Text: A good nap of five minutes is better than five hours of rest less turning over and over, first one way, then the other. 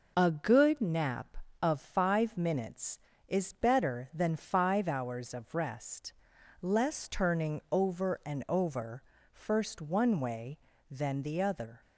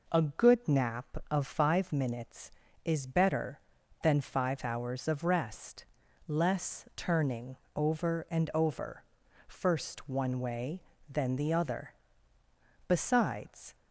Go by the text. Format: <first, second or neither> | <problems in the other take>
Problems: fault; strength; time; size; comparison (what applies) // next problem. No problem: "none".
first | pauses between "rest" and "less"; at 5.8 s; 0.42 s long; noticeable in the first // pauses between "turning" and "over"; slight; at 7.5 s; 0.20 s long // goes on to say "Besides"; noticeable; from 12.8 s on; 0.88 s long